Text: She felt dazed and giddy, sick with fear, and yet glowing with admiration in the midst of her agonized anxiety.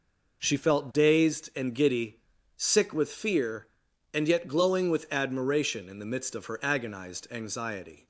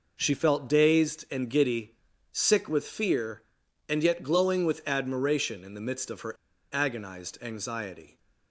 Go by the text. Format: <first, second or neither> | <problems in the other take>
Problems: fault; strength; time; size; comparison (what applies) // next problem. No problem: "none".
first | pauses between "her" and "agonized"; at 6.3 s; 0.37 s long